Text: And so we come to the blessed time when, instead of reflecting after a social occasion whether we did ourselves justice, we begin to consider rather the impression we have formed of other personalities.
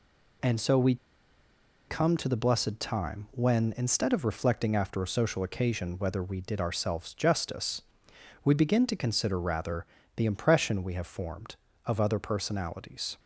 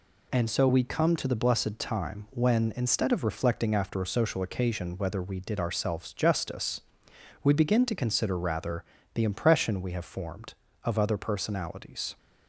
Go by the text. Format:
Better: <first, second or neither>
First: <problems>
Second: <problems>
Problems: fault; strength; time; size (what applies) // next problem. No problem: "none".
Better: second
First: pauses between "we" and "come"; noticeable; at 0.9 s; 0.92 s long // pauses between "rather" and "the"; slight; at 9.8 s; 0.30 s long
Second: pauses between "rather" and "the"; slight; at 8.8 s; 0.30 s long